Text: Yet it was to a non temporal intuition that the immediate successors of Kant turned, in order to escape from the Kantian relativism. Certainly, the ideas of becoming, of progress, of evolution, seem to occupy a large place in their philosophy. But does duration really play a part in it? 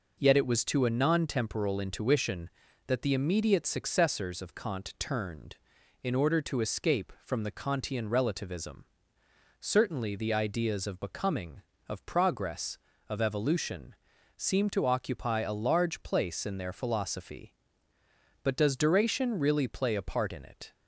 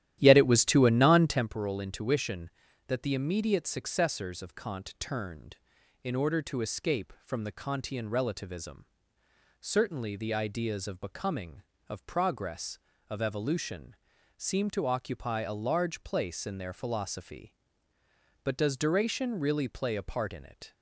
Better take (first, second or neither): first